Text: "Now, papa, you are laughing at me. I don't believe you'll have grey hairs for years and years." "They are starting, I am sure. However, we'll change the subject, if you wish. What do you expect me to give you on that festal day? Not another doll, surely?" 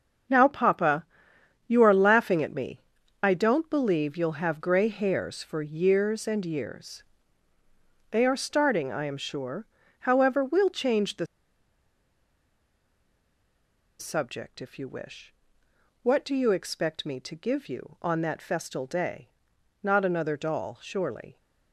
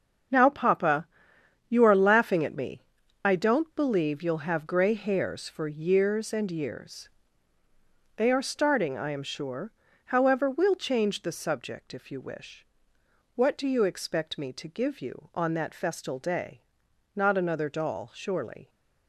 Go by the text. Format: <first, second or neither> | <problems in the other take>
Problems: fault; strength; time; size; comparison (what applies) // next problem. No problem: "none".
second | starts louder than the rest; until 1.9 s; 7 dB; also in the second // pauses between "the" and "subject"; strong; at 11.2 s; 2.7 s long